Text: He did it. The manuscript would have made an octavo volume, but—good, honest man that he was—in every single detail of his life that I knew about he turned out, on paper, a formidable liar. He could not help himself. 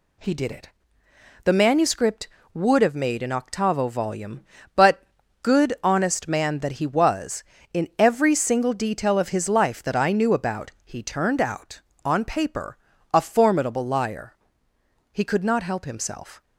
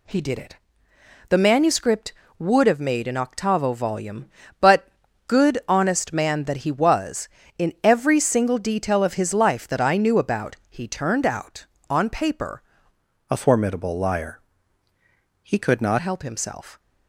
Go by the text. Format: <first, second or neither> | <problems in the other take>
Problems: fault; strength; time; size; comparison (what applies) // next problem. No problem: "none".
first | pauses between "about" and "he"; slight; at 10.5 s; 0.16 s long; slight in the first // changes voice from "a" to "not"; from 13.3 to 15.9 s; 2.6 s long